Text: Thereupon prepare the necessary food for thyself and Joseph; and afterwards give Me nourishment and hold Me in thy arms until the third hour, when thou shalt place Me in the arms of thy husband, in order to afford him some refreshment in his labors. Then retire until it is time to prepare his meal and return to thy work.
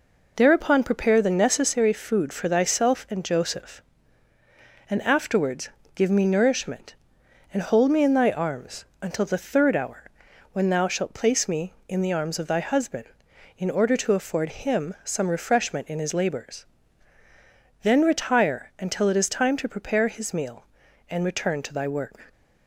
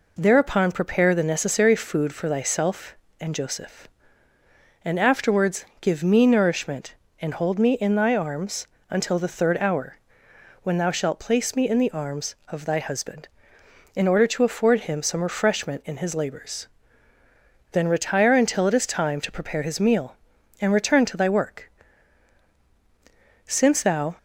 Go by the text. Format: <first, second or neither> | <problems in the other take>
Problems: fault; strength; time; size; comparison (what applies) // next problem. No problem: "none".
first | pauses between "afterwards" and "give"; slight; at 5.6 s; 0.16 s long; slight in the first // pauses between "arms" and "until"; slight; at 8.6 s; 0.24 s long; slight in the first // goes on to say "Since thou"; noticeable; from 23.4 s on; 0.70 s long